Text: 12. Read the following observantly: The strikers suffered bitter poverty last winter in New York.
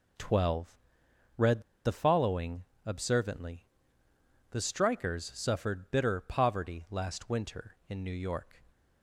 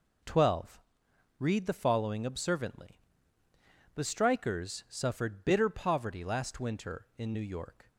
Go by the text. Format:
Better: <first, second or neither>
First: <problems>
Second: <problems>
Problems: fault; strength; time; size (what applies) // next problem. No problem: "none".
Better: second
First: pauses between "Read" and "the"; slight; at 1.6 s; 0.23 s long // pauses between "following" and "observantly"; slight; at 2.6 s; 0.22 s long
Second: none